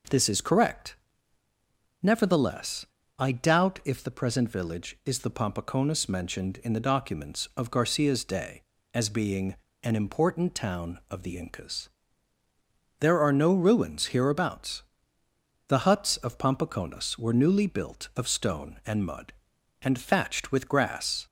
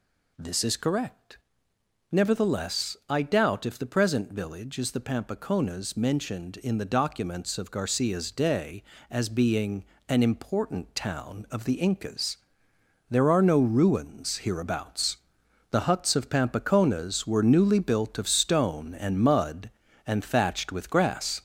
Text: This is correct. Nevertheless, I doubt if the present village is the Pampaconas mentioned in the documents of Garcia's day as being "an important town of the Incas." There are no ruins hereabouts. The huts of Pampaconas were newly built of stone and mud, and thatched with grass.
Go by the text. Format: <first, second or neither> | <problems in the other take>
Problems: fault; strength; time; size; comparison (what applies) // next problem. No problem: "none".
first | gets louder; noticeable; throughout; 4.5 dB // pauses between "being" and "an"; slight; at 9.8 s; 0.24 s long; slight in the first